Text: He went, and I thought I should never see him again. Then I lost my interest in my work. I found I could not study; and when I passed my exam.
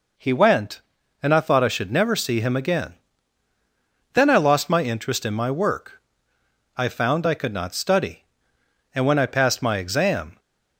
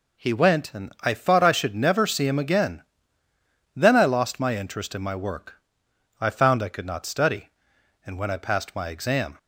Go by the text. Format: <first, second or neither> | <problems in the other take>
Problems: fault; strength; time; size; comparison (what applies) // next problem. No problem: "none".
neither | none